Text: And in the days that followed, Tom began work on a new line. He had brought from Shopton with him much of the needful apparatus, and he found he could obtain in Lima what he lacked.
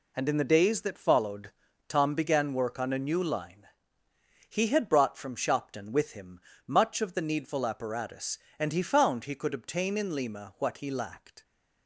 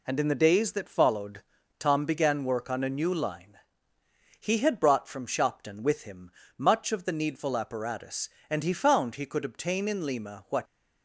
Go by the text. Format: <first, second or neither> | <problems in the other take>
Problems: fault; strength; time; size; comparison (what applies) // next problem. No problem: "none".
first | pauses between "him" and "much"; slight; at 6.3 s; 0.28 s long; slight in the first // stops before "he lacked"; at 10.6 s